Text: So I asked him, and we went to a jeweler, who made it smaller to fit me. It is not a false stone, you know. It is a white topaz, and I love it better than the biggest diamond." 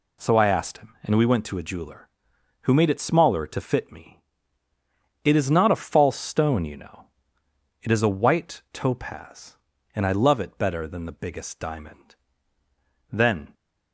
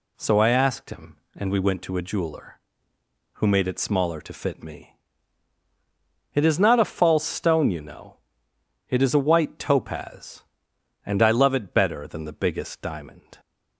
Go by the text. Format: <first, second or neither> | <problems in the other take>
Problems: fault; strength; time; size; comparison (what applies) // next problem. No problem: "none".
second | goes on to say "Then"; slight; from 13.0 s on; 0.44 s long